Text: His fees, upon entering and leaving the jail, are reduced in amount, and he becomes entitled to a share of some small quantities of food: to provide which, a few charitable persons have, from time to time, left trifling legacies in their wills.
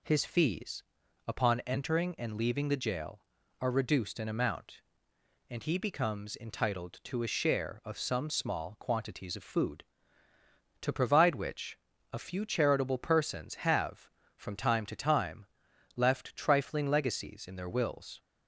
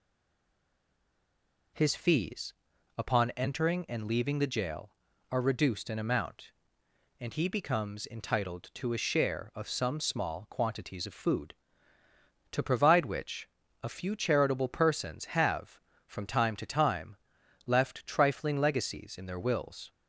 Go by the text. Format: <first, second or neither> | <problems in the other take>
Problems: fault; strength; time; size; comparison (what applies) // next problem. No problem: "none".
first | stays silent before the first word; noticeable; until 1.7 s; 1.7 s long